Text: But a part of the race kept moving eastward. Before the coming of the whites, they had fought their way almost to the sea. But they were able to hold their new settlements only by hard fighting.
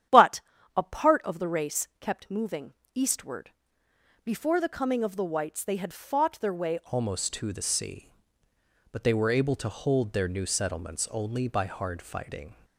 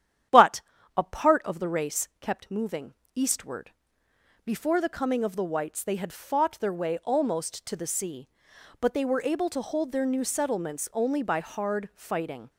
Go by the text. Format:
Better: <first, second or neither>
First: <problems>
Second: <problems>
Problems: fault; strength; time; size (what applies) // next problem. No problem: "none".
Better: second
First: starts louder than the rest; strong; until 1.4 s; 10 dB // pauses between "But" and "a"; slight; at 0.4 s; 0.34 s long // pauses between "moving" and "eastward"; slight; at 2.7 s; 0.22 s long // changes voice at "almost"; from 6.8 s on; 5.7 s long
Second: starts louder than the rest; strong; until 1.6 s; 10 dB // pauses between "But" and "a"; slight; at 0.6 s; 0.34 s long // pauses between "moving" and "eastward"; slight; at 2.9 s; 0.22 s long